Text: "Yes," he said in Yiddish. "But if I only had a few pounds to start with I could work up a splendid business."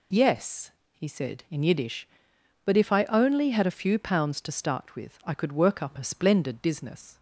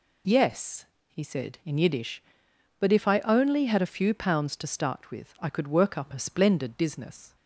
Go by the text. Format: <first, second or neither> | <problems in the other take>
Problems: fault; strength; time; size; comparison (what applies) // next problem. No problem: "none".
neither | none